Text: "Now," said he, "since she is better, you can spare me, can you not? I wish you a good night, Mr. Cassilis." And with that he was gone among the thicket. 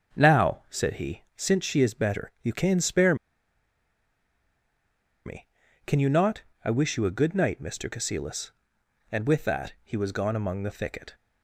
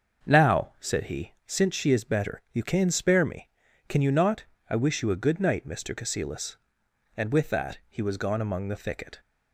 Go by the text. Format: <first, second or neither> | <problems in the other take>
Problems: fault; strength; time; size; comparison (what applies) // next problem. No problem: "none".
second | starts louder than the rest; until 1.2 s; 6.5 dB; also in the second // pauses between "spare" and "me"; strong; at 3.1 s; 2.1 s long